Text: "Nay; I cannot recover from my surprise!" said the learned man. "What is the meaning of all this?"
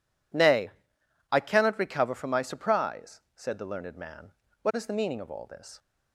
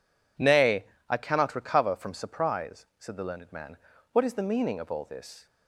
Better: first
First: none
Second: skips "my"; at 2.1 s

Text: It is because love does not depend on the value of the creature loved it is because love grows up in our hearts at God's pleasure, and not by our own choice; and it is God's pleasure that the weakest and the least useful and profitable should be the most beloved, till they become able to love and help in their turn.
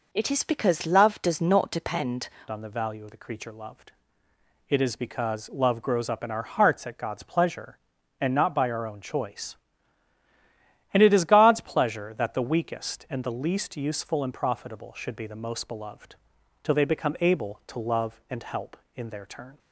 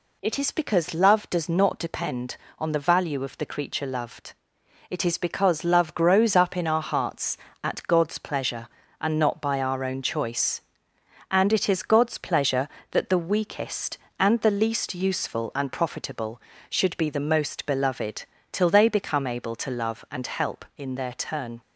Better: second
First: changes voice at "on"; from 2.5 s on; 17.0 s long // pauses between "loved" and "it"; noticeable; at 3.9 s; 0.76 s long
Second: pauses between "loved" and "it"; noticeable; at 4.3 s; 0.56 s long

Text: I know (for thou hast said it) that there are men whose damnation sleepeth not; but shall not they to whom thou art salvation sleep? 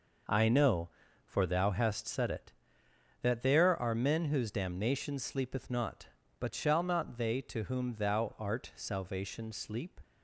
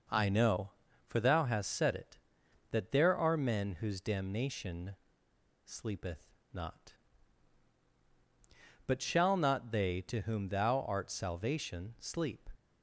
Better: first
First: none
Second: pauses between "damnation" and "sleepeth"; noticeable; at 4.9 s; 0.69 s long // pauses between "sleepeth" and "not"; slight; at 6.2 s; 0.22 s long

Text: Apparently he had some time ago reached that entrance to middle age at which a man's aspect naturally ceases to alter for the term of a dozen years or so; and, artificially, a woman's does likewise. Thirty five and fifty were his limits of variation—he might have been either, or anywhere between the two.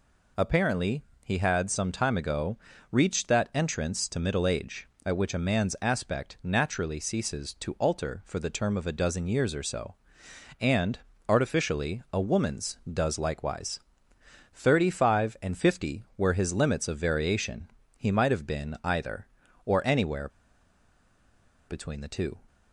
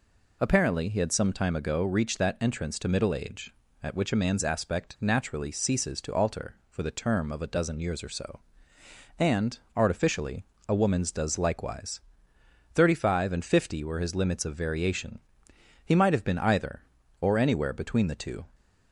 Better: second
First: pauses between "Apparently" and "he"; slight; at 1.0 s; 0.22 s long // pauses between "ago" and "reached"; slight; at 2.5 s; 0.34 s long // pauses between "anywhere" and "between"; strong; at 20.2 s; 1.3 s long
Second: none

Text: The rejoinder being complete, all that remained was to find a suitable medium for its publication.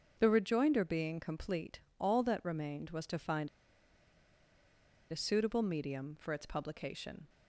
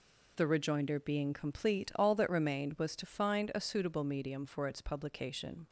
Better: second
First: starts louder than the rest; until 1.2 s; 6.5 dB // pauses between "find" and "a"; strong; at 3.4 s; 1.6 s long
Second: none

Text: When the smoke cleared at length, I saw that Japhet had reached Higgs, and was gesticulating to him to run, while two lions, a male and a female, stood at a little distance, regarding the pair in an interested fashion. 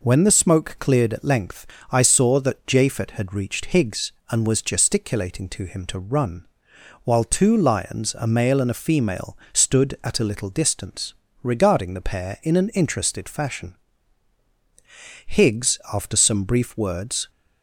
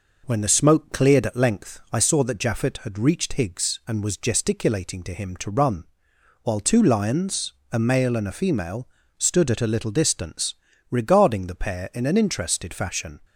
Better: second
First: goes on to say "Higgs after some brief words"; strong; from 15.2 s on; 2.0 s long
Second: none

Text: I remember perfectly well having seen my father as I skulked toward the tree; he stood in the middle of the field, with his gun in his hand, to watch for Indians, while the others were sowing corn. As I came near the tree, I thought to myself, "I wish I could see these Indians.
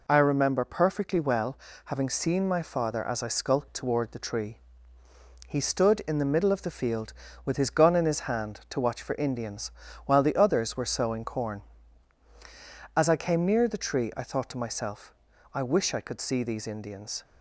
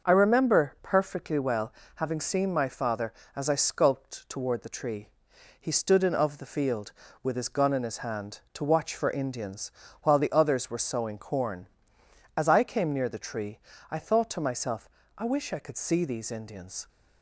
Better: first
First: pauses between "well" and "having"; slight; at 1.5 s; 0.28 s long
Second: starts louder than the rest; until 1.1 s; 6 dB // pauses between "well" and "having"; slight; at 1.7 s; 0.22 s long // skips "the middle"; at 6.1 s

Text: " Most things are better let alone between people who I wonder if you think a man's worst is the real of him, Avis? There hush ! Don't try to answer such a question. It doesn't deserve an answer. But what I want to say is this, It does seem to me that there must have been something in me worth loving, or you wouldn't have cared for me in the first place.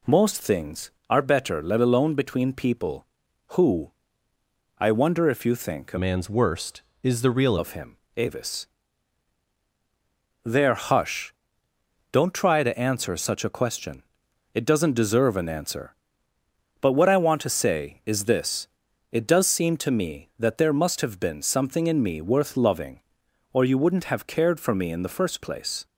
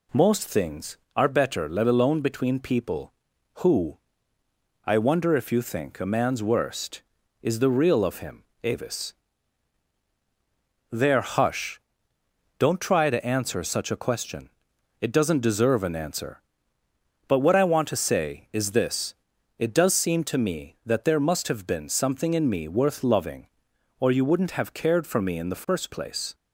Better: second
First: pauses between "who" and "I"; noticeable; at 3.9 s; 0.86 s long // changes voice from "man's" to "real"; from 5.9 to 7.5 s; 1.6 s long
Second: pauses between "who" and "I"; noticeable; at 3.9 s; 0.86 s long

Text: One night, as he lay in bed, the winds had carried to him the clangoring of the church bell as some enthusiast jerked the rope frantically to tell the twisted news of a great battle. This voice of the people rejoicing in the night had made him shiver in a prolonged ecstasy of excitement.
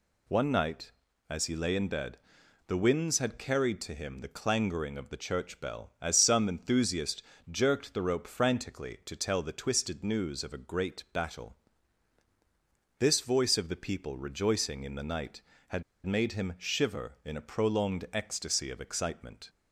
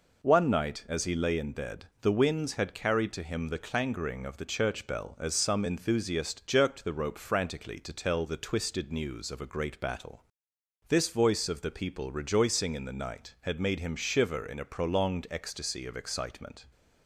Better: second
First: pauses between "enthusiast" and "jerked"; slight; at 7.2 s; 0.28 s long // pauses between "had" and "made"; slight; at 15.8 s; 0.22 s long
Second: none

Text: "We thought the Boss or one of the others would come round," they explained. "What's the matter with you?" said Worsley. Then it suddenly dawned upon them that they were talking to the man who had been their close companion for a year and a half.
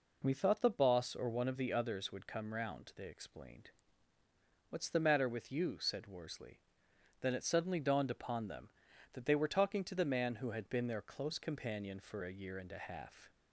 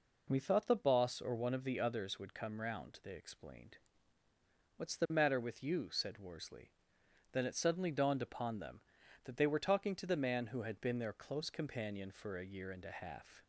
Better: neither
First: none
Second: none

